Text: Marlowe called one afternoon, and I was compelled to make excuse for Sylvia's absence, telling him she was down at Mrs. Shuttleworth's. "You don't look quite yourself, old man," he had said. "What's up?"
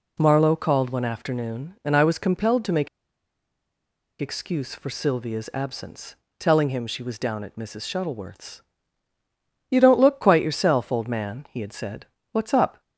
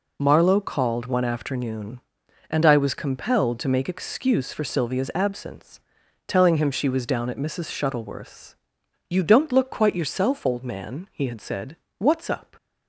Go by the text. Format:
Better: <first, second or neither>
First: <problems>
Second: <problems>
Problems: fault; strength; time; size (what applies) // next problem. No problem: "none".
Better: second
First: pauses between "make" and "excuse"; strong; at 2.8 s; 1.3 s long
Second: none